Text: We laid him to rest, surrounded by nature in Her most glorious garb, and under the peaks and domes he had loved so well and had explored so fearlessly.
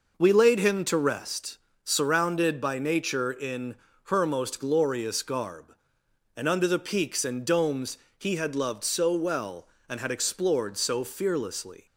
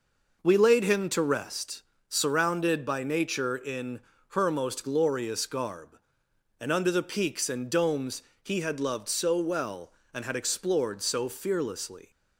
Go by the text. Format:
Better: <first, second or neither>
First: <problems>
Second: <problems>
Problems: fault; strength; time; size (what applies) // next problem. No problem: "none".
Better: neither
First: pauses between "in" and "Her"; slight; at 3.7 s; 0.30 s long // pauses between "domes" and "he"; slight; at 7.9 s; 0.22 s long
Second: pauses between "in" and "Her"; slight; at 3.9 s; 0.30 s long // pauses between "domes" and "he"; slight; at 8.2 s; 0.22 s long